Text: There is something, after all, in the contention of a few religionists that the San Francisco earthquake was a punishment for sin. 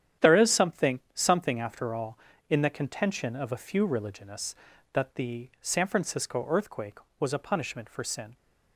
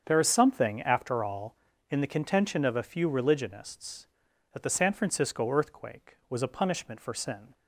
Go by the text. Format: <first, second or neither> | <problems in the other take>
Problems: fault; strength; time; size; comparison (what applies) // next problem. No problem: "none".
second | starts louder than the rest; strong; until 1.3 s; 9.5 dB; strong in the second // says "something" twice; at 1.1 s